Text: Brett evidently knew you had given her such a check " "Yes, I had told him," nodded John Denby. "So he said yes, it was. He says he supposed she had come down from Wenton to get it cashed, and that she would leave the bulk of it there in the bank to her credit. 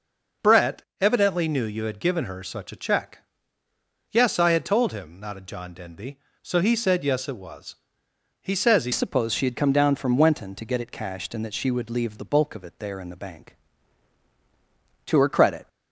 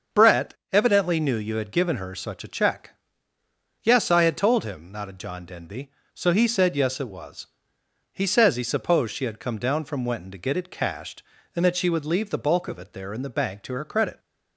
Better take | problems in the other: second | pauses between "Brett" and "evidently"; slight; at 0.8 s; 0.16 s long; slight in the second // changes voice at "supposed"; from 8.9 s on; 6.7 s long

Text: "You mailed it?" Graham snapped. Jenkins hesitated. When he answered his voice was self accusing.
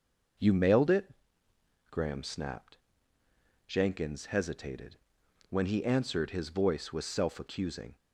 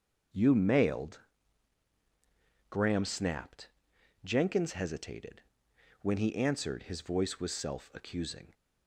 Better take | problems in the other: first | starts louder than the rest; until 2.8 s; 6.5 dB // skips "it"; at 1.9 s

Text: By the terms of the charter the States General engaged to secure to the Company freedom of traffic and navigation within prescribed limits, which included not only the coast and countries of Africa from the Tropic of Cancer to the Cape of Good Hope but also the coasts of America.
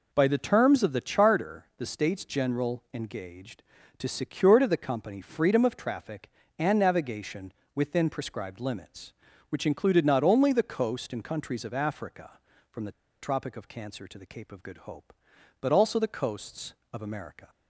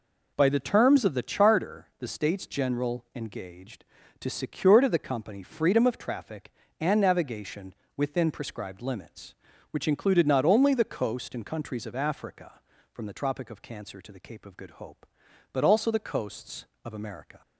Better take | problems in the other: second | pauses between "navigation" and "within"; slight; at 7.5 s; 0.22 s long; slight in the second // pauses between "the" and "Tropic"; slight; at 12.9 s; 0.29 s long

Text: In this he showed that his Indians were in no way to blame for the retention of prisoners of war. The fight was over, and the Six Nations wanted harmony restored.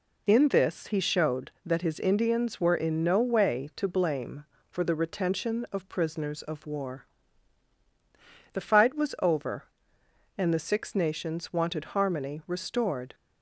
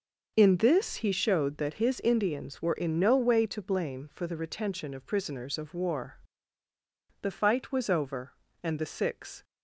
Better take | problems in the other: first | stops before "Nations wanted harmony restored"; at 9.4 s

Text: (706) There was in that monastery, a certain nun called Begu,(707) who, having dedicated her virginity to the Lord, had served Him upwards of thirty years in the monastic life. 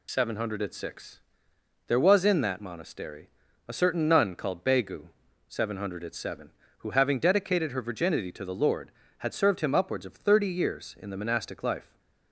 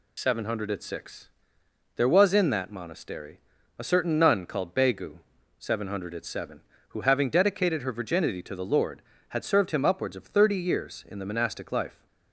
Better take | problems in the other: neither | none

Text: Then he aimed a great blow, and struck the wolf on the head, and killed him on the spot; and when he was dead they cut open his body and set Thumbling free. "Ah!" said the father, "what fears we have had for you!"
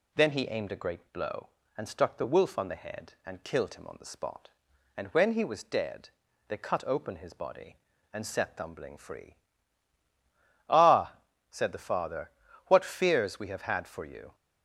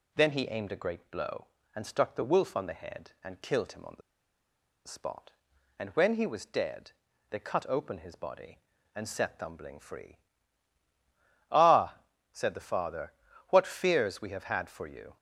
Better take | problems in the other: first | pauses between "the" and "spot"; noticeable; at 4.0 s; 0.85 s long // pauses between "dead" and "they"; slight; at 6.9 s; 0.36 s long; slight in the first

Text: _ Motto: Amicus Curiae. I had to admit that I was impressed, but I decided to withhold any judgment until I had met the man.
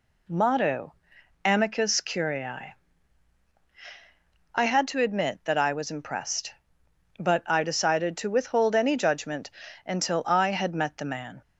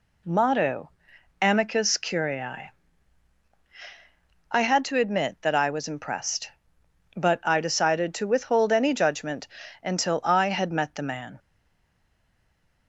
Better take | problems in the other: first | pauses between "judgment" and "until"; slight; at 9.4 s; 0.34 s long; slight in the first // stays silent after the last word; noticeable; from 11.3 s on; 1.5 s long

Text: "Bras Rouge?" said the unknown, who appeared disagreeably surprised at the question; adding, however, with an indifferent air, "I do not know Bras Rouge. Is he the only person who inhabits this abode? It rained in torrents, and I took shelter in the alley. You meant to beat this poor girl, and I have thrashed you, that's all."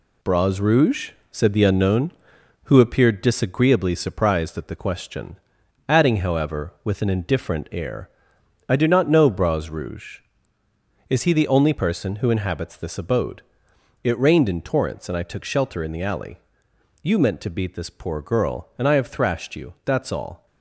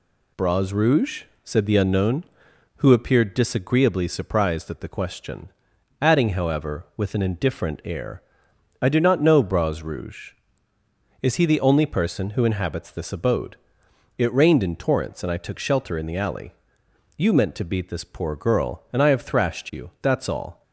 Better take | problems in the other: second | gets quieter; throughout; 6.5 dB

